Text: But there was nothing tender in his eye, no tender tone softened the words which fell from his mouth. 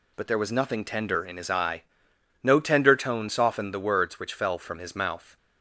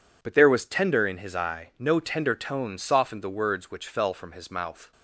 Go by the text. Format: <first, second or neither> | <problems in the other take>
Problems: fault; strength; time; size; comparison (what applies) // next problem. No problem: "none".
first | skips "nothing"; at 0.6 s